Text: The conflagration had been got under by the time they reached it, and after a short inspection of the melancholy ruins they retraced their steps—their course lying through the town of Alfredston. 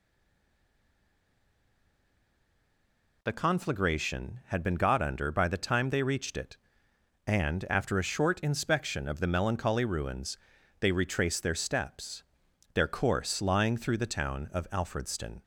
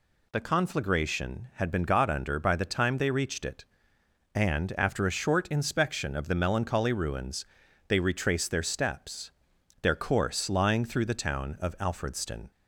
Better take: second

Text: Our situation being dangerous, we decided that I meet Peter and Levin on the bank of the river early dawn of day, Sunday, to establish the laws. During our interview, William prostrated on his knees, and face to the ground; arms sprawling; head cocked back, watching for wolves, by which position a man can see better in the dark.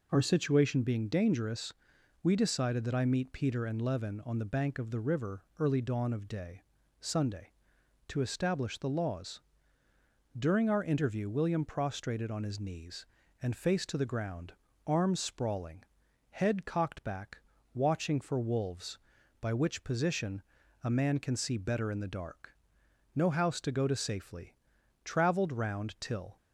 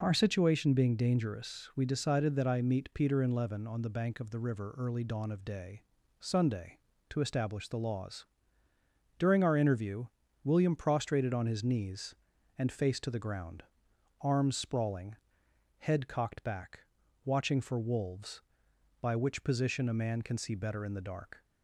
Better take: second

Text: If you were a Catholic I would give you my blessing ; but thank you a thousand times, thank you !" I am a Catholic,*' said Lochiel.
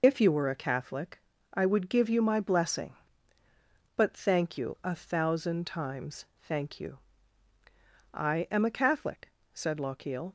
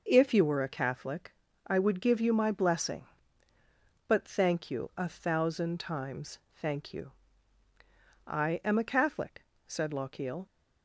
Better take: second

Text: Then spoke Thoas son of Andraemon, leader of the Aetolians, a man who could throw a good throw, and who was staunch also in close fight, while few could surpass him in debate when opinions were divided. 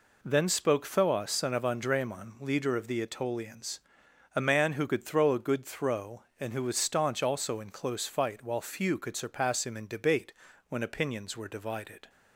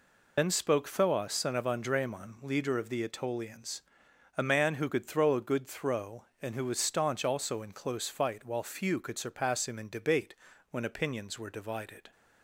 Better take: first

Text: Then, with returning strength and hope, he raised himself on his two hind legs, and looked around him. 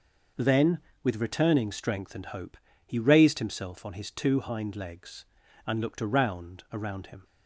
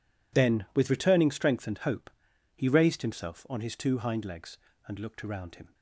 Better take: second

